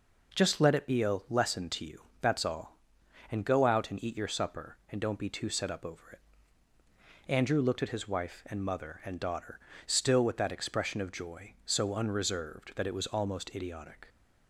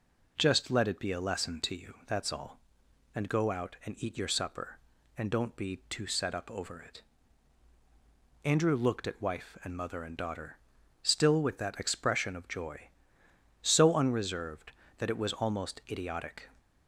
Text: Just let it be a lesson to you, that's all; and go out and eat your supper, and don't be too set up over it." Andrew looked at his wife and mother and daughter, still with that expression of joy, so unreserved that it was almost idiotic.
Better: first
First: none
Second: skips "his"; at 9.2 s

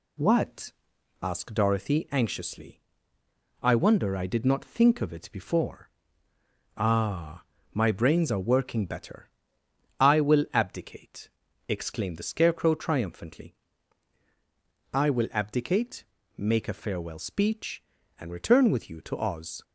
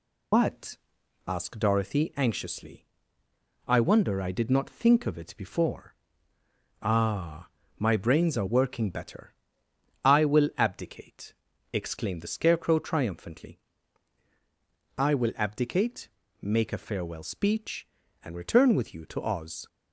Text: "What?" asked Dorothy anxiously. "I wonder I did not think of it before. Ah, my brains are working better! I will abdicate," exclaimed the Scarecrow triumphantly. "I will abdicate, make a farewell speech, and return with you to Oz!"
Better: first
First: none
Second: loses the start of "What"; at 0.3 s; 95 ms

